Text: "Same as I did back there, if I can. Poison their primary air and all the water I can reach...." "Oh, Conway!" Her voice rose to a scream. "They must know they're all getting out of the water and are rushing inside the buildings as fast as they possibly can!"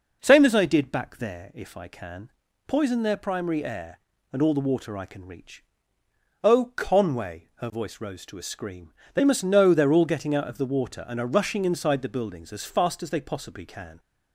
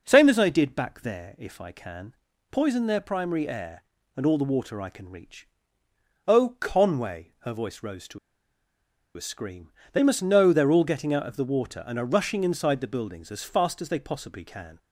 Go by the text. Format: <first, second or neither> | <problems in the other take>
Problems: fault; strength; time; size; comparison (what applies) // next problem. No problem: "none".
first | pauses between "to" and "a"; noticeable; at 8.1 s; 0.97 s long